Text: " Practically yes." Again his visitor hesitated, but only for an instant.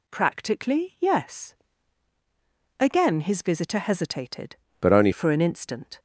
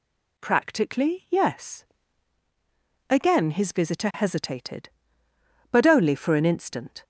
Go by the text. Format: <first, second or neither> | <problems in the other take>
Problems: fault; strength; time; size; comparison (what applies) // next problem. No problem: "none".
second | changes voice from "but" to "only"; from 4.7 to 5.1 s; 0.4 s long